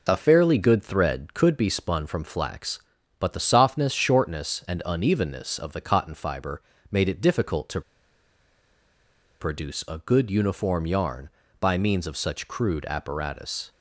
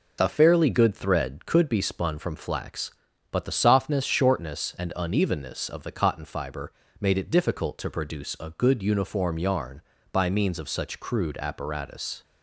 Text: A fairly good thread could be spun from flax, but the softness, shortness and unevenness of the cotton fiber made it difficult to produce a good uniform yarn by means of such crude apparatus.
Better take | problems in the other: second | pauses between "fiber" and "made"; slight; at 6.6 s; 0.28 s long; slight in the second // pauses between "to" and "produce"; strong; at 7.8 s; 1.5 s long

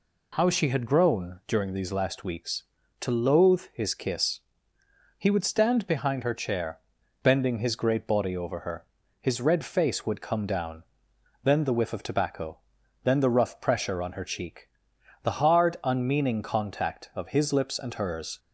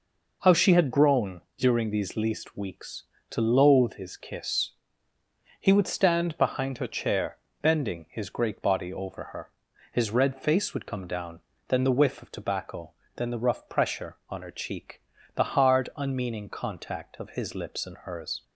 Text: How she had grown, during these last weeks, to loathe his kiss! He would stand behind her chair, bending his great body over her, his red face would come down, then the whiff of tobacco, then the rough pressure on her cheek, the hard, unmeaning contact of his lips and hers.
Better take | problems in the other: first | says "least" for "last"; at 2.1 s

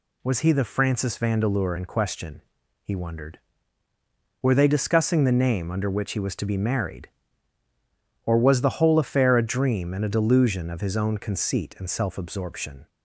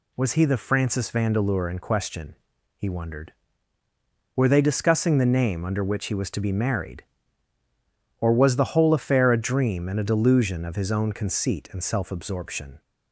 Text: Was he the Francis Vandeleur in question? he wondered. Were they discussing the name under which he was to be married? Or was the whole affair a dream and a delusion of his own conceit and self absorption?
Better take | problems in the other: neither | none

